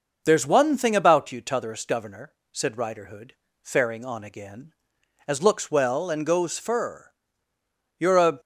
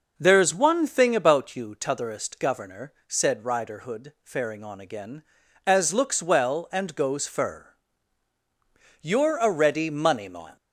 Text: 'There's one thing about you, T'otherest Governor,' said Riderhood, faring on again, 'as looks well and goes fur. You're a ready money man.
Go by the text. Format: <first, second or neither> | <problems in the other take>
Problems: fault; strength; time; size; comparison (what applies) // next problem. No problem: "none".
second | stops before "ready money man"; at 8.3 s